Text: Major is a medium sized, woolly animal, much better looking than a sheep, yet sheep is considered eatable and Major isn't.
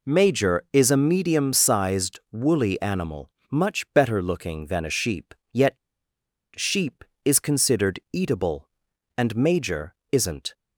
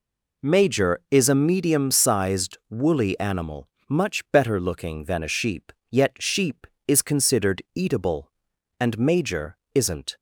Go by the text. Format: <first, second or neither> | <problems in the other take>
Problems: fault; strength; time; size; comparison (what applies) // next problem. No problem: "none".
second | pauses between "yet" and "sheep"; noticeable; at 5.7 s; 0.79 s long // pauses between "Major" and "isn't"; slight; at 9.9 s; 0.16 s long; slight in the second